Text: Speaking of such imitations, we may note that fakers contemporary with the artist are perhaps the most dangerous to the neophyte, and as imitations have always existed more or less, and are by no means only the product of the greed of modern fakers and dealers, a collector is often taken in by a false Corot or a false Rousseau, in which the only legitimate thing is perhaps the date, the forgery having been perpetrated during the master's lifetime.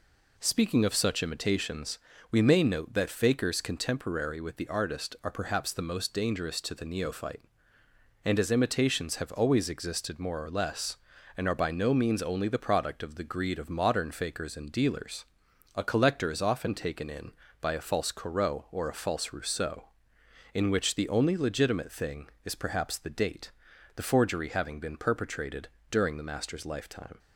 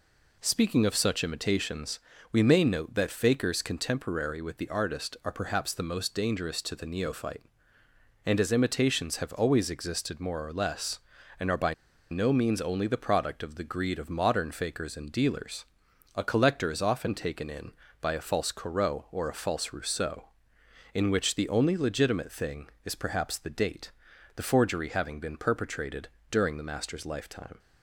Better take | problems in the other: first | pauses between "by" and "no"; at 11.7 s; 0.36 s long // pauses between "perpetrated" and "during"; slight; at 26.0 s; 0.22 s long; slight in the first

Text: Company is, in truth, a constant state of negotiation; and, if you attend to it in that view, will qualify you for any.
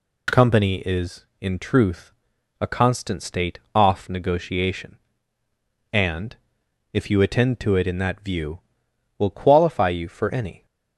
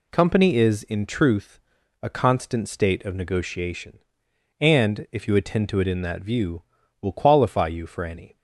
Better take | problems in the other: second | says "off" for "of"; at 3.7 s

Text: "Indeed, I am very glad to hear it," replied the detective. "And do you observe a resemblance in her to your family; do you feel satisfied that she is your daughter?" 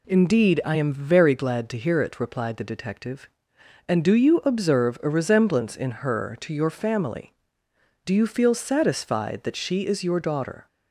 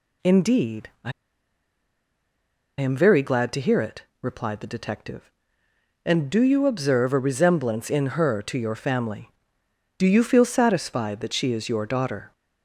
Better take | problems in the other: first | pauses between "I" and "am"; strong; at 1.1 s; 1.6 s long

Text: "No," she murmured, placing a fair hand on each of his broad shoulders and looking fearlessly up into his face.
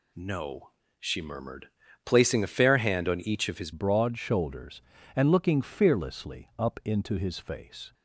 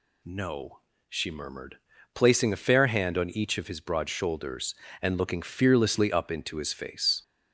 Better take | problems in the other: second | changes voice at "broad"; from 3.7 s on; 4.2 s long

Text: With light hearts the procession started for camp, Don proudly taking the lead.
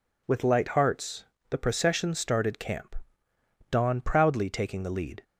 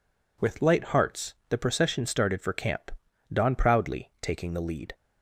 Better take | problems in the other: second | pauses between "hearts" and "the"; slight; at 1.2 s; 0.24 s long; slight in the second // skips "for"; at 2.5 s

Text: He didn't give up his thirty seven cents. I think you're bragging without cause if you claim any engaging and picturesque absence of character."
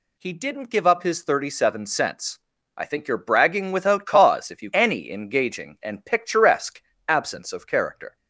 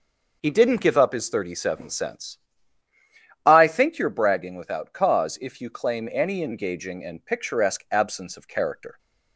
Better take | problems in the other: second | skips "claim"; at 4.7 s // pauses between "picturesque" and "absence"; slight; at 6.8 s; 0.26 s long

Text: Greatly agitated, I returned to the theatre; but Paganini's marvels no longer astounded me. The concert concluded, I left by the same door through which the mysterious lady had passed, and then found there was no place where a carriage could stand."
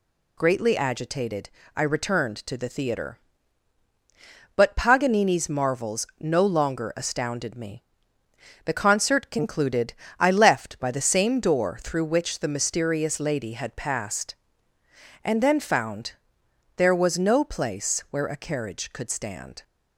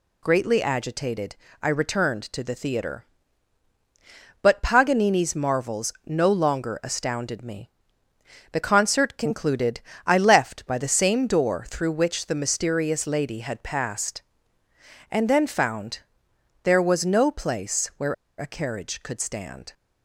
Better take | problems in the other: first | pauses between "found" and "there"; noticeable; at 15.9 s; 0.62 s long; noticeable in the first // pauses between "where" and "a"; slight; at 18.1 s; 0.24 s long

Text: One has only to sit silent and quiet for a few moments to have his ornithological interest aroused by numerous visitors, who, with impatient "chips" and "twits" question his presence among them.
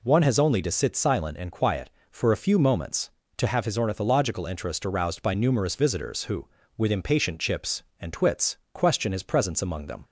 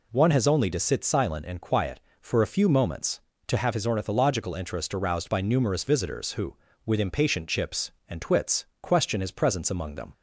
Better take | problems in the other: neither | pauses between "twits" and "question"; slight; the same in both

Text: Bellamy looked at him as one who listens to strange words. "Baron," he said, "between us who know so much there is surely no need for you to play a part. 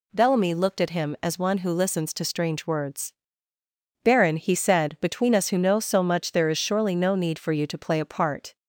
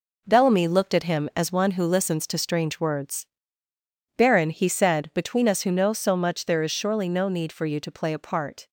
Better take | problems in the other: first | gets quieter; strong; throughout; 8.5 dB

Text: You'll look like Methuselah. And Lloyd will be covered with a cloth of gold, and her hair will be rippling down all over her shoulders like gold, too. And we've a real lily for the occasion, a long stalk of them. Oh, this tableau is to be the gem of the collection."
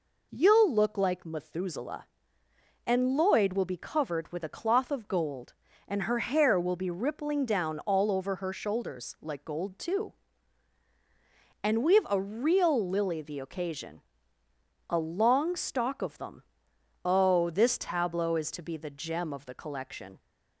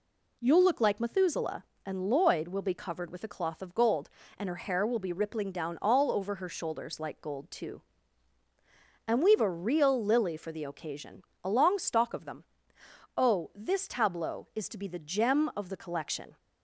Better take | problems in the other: second | skips "for"; at 13.2 s

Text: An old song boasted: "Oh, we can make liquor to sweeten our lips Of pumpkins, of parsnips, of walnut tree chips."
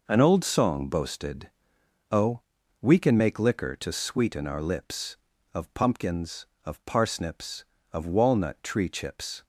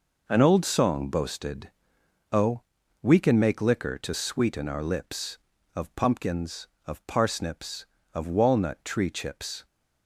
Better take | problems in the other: neither | none

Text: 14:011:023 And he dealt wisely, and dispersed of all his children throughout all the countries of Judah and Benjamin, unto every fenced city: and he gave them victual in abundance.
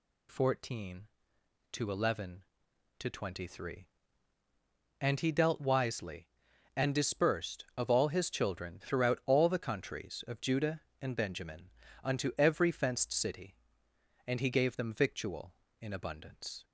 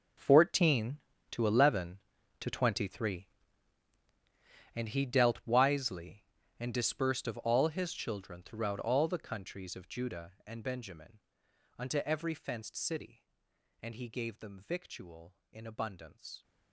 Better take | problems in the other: first | gets quieter; strong; throughout; 15 dB

